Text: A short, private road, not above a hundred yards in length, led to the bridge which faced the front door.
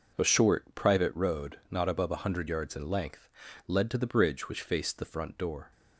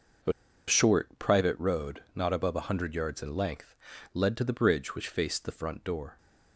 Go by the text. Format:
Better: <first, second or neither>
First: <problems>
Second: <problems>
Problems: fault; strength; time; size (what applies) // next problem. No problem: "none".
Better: first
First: none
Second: pauses between "A" and "short"; slight; at 0.3 s; 0.36 s long